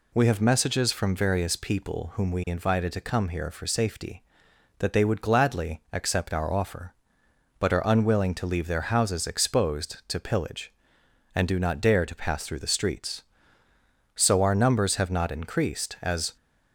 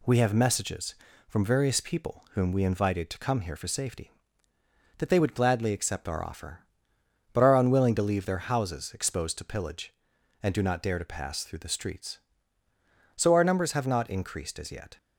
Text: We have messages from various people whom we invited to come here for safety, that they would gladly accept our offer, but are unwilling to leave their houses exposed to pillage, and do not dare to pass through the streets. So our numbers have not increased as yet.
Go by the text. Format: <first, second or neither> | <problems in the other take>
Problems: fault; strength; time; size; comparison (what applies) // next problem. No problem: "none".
second | stops before "yet"; at 16.3 s